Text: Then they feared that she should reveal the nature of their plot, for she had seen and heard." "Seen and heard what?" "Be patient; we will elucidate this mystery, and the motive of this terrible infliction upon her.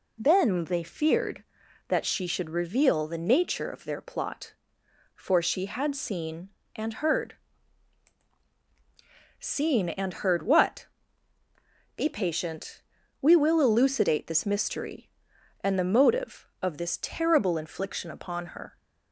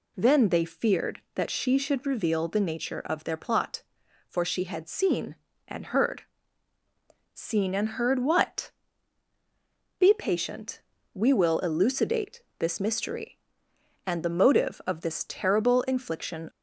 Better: first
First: none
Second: pauses between "elucidate" and "this"; slight; at 12.4 s; 0.16 s long // stops before "upon her"; at 16.5 s

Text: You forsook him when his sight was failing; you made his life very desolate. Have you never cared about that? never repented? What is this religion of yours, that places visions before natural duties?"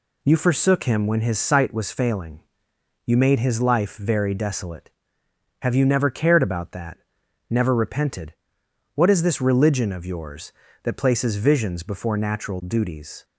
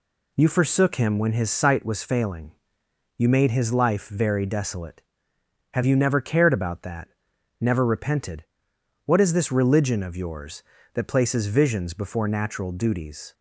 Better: neither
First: none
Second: none

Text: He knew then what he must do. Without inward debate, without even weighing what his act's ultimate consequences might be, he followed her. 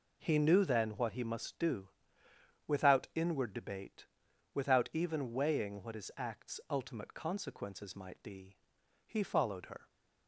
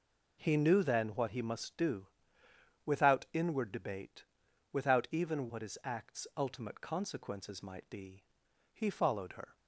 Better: first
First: none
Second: skips "weighing"; at 5.4 s

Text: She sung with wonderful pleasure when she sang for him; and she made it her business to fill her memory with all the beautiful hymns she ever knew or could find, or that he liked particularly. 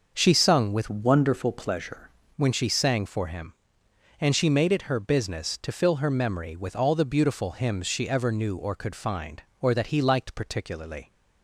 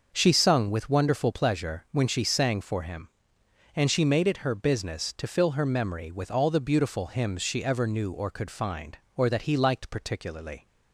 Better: second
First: starts louder than the rest; noticeable; until 1.1 s; 6 dB // changes voice from "wonderful" to "pleasure"; from 0.8 to 2.0 s; 1.2 s long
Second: starts louder than the rest; until 1.1 s; 6 dB

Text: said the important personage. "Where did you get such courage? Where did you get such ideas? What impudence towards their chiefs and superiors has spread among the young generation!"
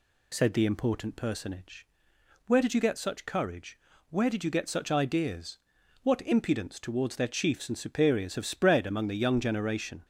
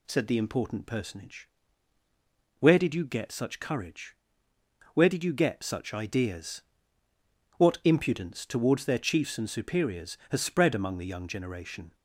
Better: second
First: says "have" for "has"; at 8.3 s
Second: none

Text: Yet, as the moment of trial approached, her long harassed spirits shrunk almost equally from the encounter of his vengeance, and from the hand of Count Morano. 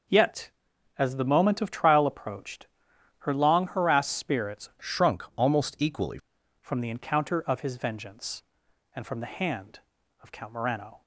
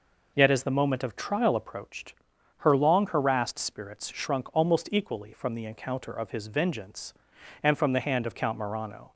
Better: second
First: changes voice from "shrunk" to "equally"; from 4.8 to 6.1 s; 1.3 s long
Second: none

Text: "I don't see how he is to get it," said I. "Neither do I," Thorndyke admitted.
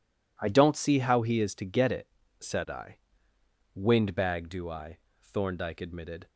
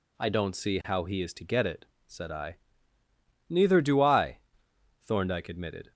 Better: second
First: says "Windbag" for "Neither"; at 3.7 s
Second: none

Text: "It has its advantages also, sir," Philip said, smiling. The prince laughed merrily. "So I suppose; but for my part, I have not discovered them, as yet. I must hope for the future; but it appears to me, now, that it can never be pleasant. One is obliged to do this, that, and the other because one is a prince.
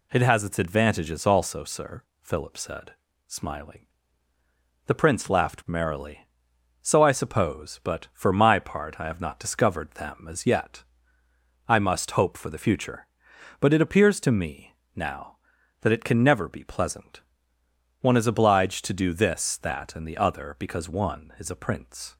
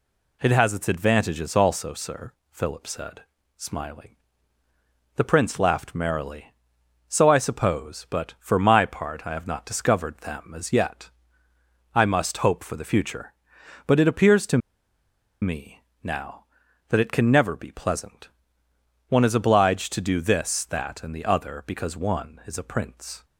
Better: first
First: none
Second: pauses between "to" and "me"; noticeable; at 14.5 s; 0.82 s long

